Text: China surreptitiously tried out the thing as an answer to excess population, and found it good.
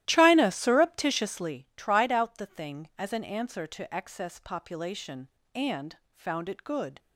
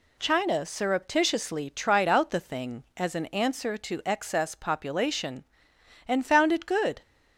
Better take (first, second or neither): second